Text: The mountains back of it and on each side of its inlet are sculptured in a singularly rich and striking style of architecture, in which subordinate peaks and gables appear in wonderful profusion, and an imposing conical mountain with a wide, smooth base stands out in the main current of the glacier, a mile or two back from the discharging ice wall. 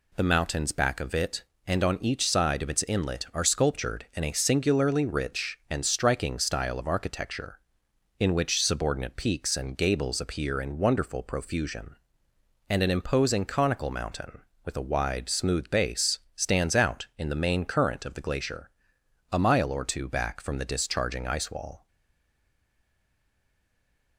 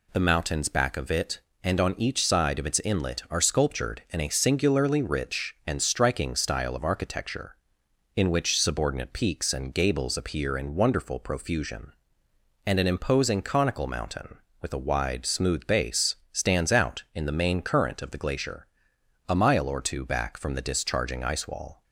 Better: second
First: pauses between "base" and "stands"; slight; at 16.1 s; 0.16 s long // stays silent after the last word; from 21.8 s on; 2.3 s long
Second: pauses between "base" and "stands"; slight; at 16.1 s; 0.16 s long

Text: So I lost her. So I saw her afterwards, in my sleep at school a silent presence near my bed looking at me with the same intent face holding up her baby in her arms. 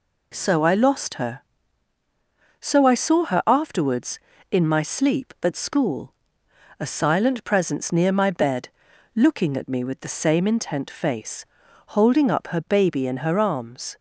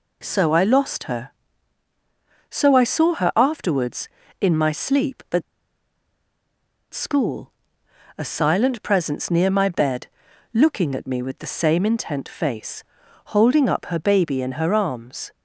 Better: first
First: pauses between "school" and "a"; noticeable; at 6.1 s; 0.66 s long // pauses between "bed" and "looking"; noticeable; at 8.6 s; 0.46 s long // pauses between "face" and "holding"; at 11.4 s; 0.44 s long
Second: pauses between "at" and "school"; strong; at 5.4 s; 1.5 s long // pauses between "school" and "a"; noticeable; at 7.5 s; 0.66 s long // pauses between "bed" and "looking"; noticeable; at 10.0 s; 0.46 s long // pauses between "face" and "holding"; at 12.8 s; 0.44 s long

